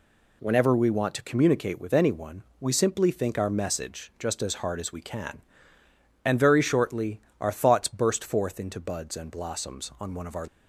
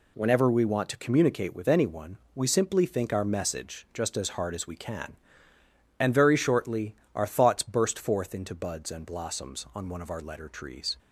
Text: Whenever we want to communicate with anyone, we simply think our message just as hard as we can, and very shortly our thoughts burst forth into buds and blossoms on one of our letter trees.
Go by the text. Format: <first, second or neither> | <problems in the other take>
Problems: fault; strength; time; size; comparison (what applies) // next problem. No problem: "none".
second | pauses between "shortly" and "our"; slight; at 7.1 s; 0.22 s long; slight in the second // stops before "letter trees"; at 10.4 s